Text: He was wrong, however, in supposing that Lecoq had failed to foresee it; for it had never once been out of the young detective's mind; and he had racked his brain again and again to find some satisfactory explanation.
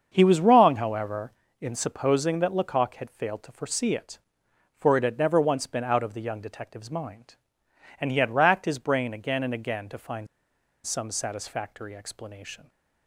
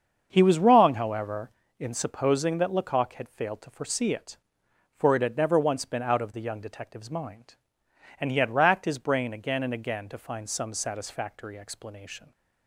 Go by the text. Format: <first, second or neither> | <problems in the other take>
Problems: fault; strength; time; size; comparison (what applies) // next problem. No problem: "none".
second | starts louder than the rest; until 1.1 s; 7 dB; also in the second // pauses between "find" and "some"; noticeable; at 10.2 s; 0.57 s long